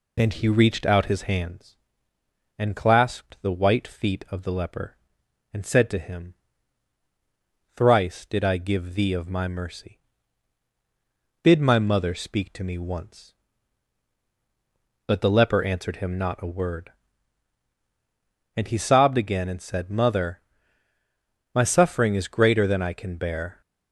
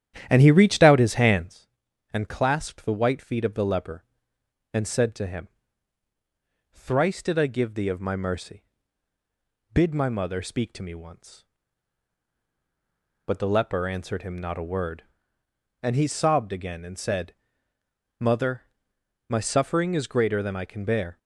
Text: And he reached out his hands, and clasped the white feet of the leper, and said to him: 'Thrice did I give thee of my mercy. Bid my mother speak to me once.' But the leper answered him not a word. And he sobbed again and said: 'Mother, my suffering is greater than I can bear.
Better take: first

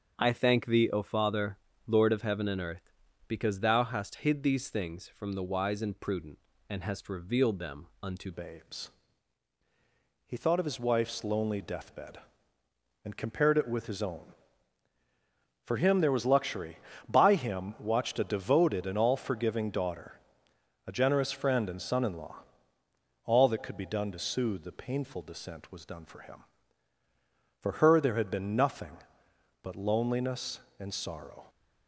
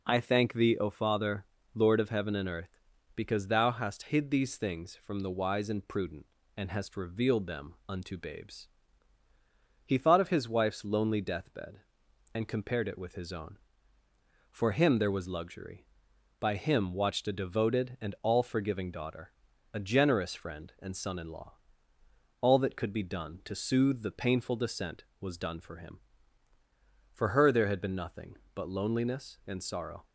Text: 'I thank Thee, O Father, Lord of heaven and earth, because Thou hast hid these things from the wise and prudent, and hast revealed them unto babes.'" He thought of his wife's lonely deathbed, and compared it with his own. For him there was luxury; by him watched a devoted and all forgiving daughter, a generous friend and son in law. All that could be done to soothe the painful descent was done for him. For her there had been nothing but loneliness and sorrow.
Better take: second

